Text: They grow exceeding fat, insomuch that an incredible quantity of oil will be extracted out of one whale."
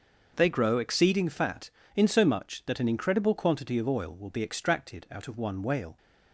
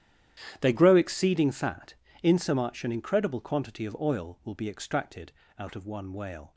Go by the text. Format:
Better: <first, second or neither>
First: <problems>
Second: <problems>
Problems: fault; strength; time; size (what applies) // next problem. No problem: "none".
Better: first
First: starts louder than the rest; noticeable; until 1.3 s; 6 dB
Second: starts louder than the rest; strong; until 1.6 s; 11 dB // skips "that"; at 2.8 s // pauses between "extracted" and "out"; slight; at 5.3 s; 0.26 s long